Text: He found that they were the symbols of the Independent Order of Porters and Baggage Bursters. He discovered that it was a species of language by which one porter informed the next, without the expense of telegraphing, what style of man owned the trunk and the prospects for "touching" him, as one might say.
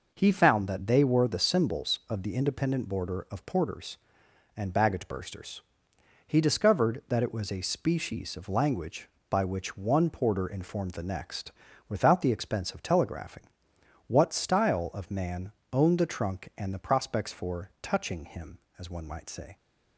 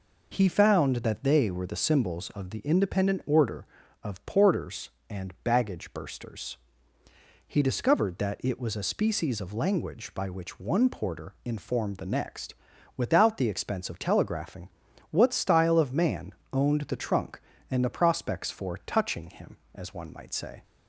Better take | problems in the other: second | says "Border" for "Order"; at 2.8 s // pauses between "man" and "owned"; slight; at 15.5 s; 0.20 s long; slight in the second

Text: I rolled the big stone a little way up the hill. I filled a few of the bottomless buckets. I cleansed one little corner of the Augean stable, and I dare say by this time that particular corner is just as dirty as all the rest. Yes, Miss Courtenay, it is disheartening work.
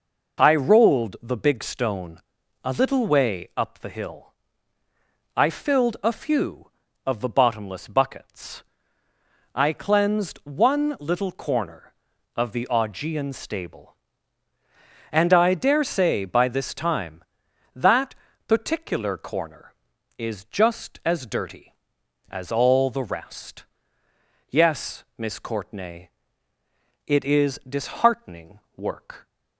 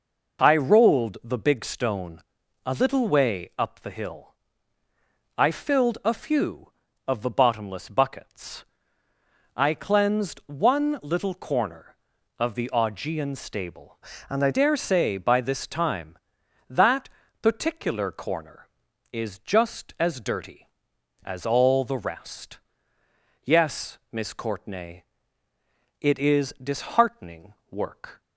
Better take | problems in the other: first | pauses between "stone" and "a"; at 2.2 s; 0.42 s long; also in the first // changes voice from "and" to "I"; from 14.2 to 14.4 s; 0.2 s long // pauses between "that" and "particular"; slight; at 17.0 s; 0.32 s long; slight in the first // pauses between "disheartening" and "work"; slight; at 27.5 s; 0.16 s long; slight in the first

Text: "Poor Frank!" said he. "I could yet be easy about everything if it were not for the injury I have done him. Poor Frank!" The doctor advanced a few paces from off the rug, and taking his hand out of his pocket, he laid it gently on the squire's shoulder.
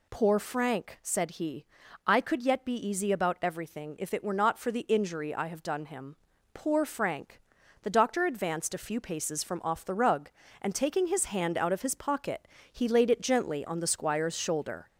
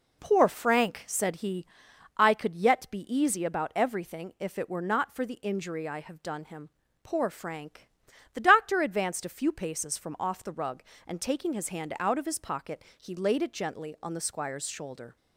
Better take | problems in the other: second | gets louder; slight; throughout; 2.5 dB

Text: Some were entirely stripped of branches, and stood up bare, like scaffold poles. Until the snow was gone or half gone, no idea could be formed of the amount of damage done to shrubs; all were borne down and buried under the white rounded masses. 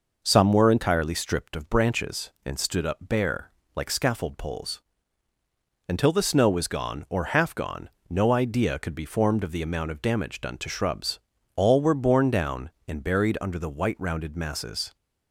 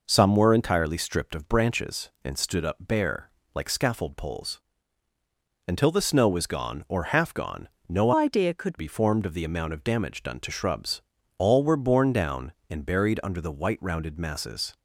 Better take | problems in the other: first | changes voice from "idea" to "could"; from 8.1 to 8.7 s; 0.6 s long

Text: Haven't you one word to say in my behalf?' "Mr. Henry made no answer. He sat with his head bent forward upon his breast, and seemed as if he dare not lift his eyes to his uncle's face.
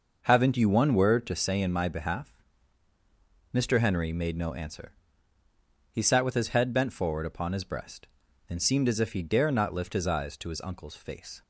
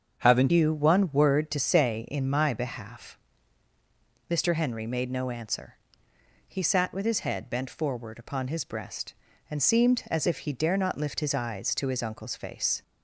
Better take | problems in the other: first | starts louder than the rest; strong; until 1.2 s; 7.5 dB // changes voice at "you"; from 0.4 s on; 12.4 s long

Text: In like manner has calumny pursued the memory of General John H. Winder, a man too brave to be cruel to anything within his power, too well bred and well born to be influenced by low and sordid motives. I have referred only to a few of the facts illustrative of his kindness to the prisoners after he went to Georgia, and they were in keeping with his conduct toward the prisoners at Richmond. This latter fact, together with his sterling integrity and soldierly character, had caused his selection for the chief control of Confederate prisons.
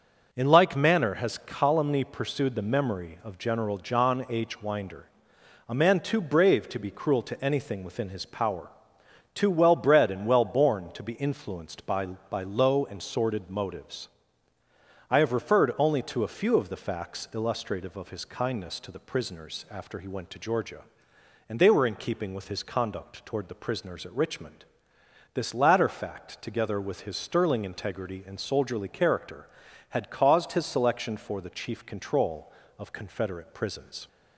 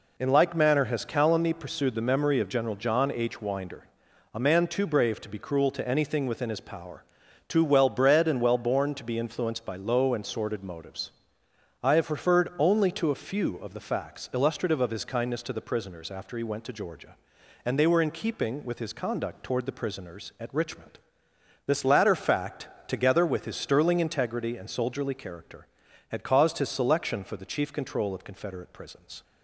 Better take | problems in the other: second | says "by" twice; at 12.2 s

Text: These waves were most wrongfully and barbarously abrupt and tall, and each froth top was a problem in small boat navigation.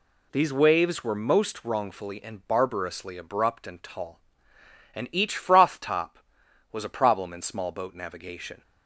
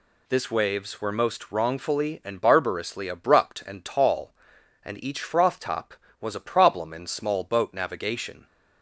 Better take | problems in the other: first | says "This" for "These"; at 0.2 s

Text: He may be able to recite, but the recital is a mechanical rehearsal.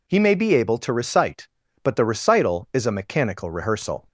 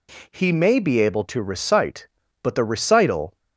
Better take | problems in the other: first | stops before "is a mechanical rehearsal"; at 3.3 s

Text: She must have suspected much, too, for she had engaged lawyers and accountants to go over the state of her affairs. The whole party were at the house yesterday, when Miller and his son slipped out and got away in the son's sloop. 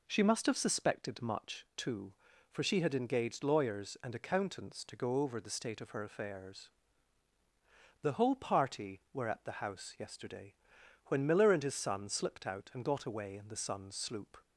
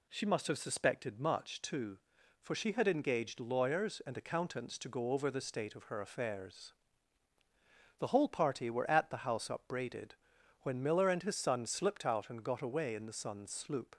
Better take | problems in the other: first | says "upbraided" for "yesterday"; at 9.5 s

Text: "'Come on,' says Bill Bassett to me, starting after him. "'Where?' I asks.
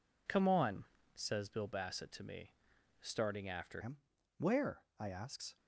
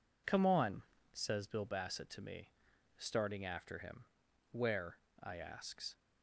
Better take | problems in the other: second | changes voice at "him"; from 3.8 s on; 1.7 s long

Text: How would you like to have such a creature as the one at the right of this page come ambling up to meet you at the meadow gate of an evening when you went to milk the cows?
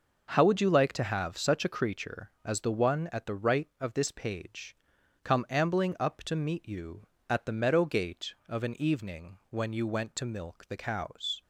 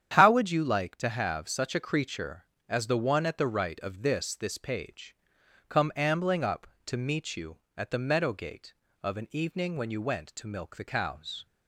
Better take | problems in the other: first | starts louder than the rest; strong; until 1.1 s; 9 dB // says "this" twice; at 4.3 s // pauses between "page" and "come"; noticeable; at 5.1 s; 0.54 s long; noticeable in the first

